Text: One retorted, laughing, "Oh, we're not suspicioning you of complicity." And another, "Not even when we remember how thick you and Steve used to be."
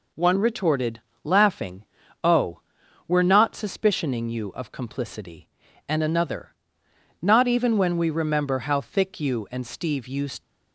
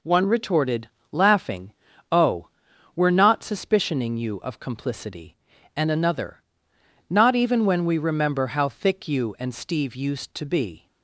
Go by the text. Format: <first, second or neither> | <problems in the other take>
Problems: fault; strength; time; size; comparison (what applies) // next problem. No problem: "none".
second | stops before "to be"; at 10.4 s